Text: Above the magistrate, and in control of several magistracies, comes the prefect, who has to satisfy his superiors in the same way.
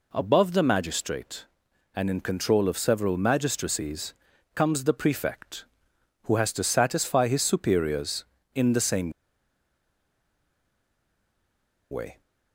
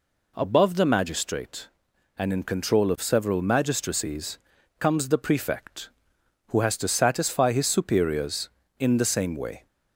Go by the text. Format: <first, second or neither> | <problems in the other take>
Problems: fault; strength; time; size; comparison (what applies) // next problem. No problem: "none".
second | pauses between "same" and "way"; strong; at 9.0 s; 2.8 s long